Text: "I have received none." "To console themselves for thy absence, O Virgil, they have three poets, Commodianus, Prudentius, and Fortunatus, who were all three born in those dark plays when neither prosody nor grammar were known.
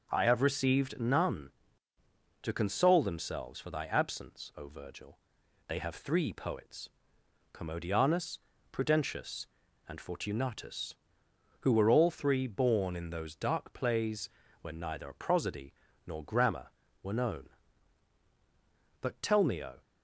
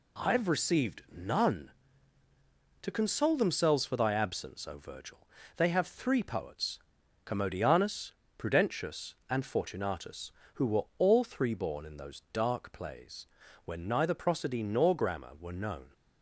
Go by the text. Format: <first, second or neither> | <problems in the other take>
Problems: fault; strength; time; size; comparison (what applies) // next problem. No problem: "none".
second | pauses between "plays" and "when"; slight; at 14.2 s; 0.32 s long; also in the second // pauses between "prosody" and "nor"; slight; at 15.7 s; 0.32 s long // goes on to say "But tell me O"; noticeable; from 19.0 s on; 0.80 s long